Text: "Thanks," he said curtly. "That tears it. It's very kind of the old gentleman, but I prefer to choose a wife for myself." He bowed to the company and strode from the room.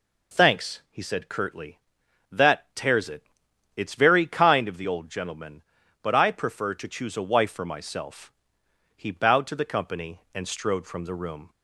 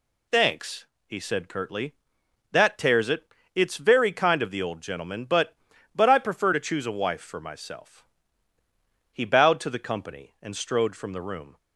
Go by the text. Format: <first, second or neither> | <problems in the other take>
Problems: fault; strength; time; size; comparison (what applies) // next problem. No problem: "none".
first | says "but" twice; at 5.9 s